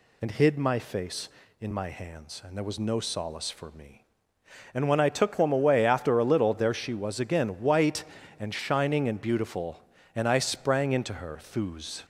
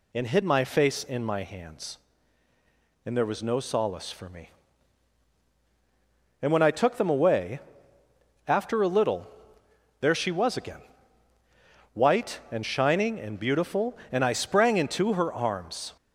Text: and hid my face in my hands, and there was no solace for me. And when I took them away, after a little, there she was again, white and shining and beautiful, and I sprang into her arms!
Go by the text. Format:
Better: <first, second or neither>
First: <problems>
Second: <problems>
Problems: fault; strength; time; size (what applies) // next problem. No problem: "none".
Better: second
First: says "thuz" for "arms"; at 11.4 s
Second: none